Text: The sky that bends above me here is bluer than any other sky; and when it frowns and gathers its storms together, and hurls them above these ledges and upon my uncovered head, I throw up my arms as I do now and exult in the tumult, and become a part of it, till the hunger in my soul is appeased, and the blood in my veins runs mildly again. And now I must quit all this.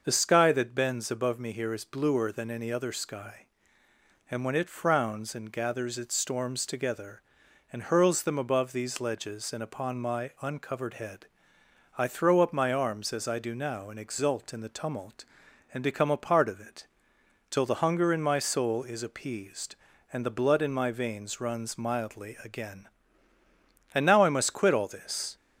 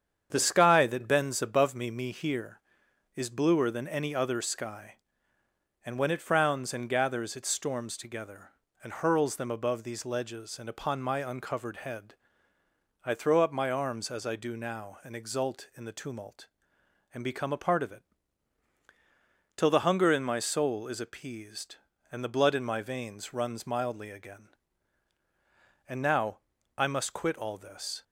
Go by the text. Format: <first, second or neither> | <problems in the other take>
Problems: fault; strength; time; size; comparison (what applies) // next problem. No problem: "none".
first | starts louder than the rest; strong; until 1.3 s; 8 dB; also in the first // says "me" twice; at 1.9 s // pauses between "now" and "I"; at 26.3 s; 0.38 s long